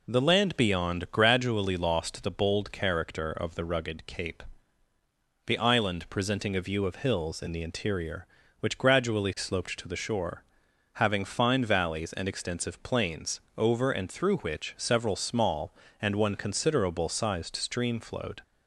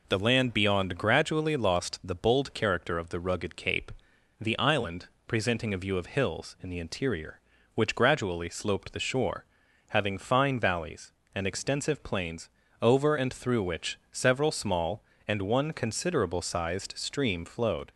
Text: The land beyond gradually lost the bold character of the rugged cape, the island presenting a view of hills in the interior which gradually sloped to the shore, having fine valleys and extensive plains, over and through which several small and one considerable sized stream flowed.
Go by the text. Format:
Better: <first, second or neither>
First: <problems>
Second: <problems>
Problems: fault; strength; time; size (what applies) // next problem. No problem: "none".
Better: first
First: none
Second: pauses between "island" and "presenting"; slight; at 5.0 s; 0.18 s long // skips "to"; at 8.9 s